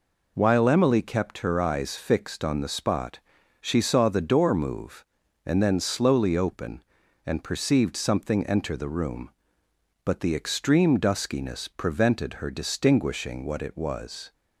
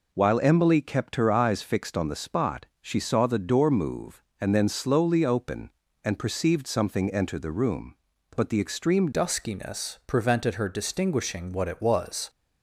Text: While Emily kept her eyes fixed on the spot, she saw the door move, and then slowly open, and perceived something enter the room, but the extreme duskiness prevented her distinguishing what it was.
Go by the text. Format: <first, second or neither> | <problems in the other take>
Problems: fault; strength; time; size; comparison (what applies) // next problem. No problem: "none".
first | changes voice at "duskiness"; from 9.1 s on; 3.1 s long